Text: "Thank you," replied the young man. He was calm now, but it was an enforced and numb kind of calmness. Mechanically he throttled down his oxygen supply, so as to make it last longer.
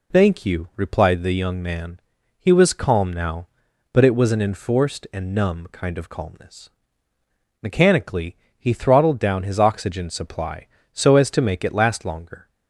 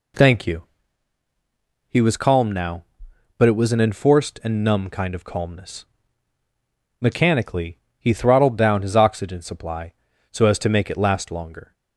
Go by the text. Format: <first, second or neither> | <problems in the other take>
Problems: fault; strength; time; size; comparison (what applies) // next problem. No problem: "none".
first | skips "replied the young man"; at 1.2 s // pauses between "Mechanically" and "he"; slight; at 7.7 s; 0.20 s long; slight in the first